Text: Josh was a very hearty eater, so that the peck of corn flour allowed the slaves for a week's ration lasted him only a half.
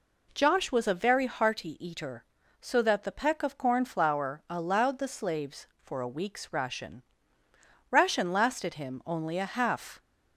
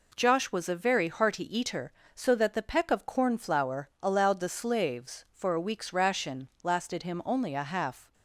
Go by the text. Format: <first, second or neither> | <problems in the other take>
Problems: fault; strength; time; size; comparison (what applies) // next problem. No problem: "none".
second | says "ration" twice; at 7.9 s